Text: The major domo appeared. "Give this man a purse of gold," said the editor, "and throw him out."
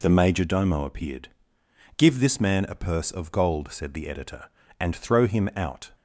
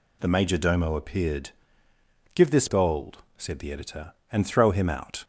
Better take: first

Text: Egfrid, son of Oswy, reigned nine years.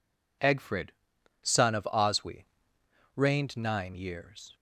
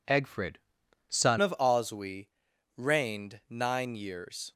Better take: first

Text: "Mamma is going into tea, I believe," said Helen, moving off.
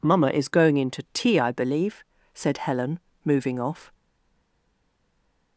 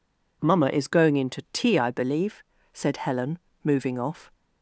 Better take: second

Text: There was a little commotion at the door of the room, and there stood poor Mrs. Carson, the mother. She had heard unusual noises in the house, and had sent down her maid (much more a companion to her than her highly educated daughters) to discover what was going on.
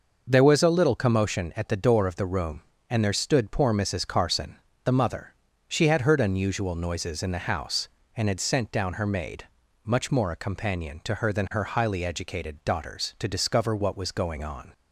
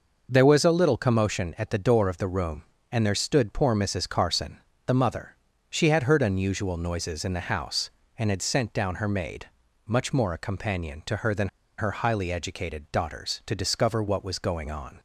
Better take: first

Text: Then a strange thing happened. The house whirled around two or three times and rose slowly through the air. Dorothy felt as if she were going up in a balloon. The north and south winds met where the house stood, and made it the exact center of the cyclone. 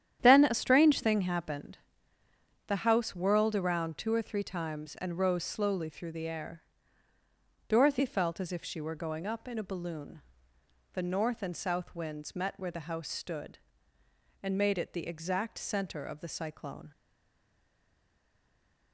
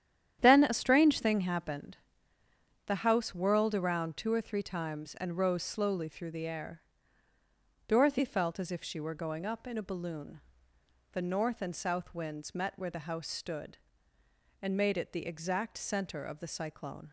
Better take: second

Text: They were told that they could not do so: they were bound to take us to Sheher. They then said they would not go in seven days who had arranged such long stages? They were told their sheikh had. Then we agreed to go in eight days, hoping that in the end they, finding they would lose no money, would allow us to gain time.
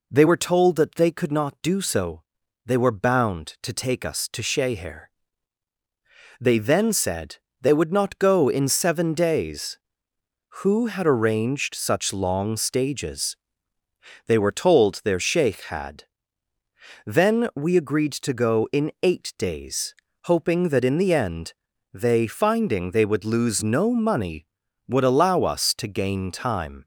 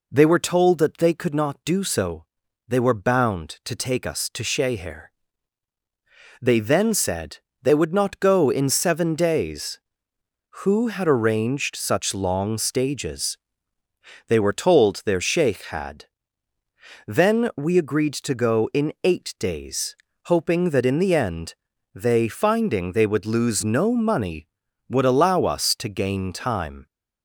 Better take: neither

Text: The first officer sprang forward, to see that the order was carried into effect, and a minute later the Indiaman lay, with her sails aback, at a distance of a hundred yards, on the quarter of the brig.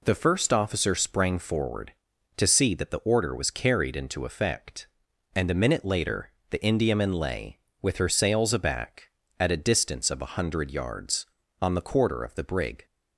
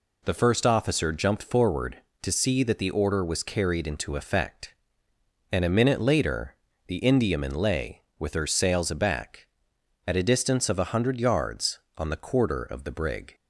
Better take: first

